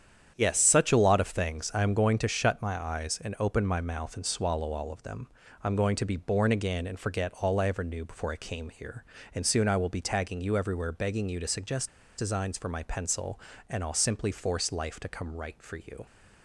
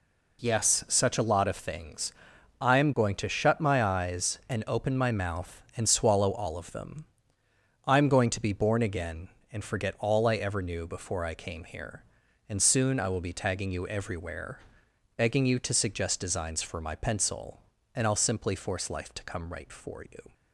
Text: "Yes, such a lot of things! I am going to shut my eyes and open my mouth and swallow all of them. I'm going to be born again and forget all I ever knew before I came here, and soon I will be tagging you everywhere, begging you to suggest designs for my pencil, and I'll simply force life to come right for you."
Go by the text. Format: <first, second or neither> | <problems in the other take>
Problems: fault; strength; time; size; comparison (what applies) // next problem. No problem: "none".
second | starts louder than the rest; strong; until 1.3 s; 8.5 dB // pauses between "suggest" and "designs"; slight; at 11.8 s; 0.30 s long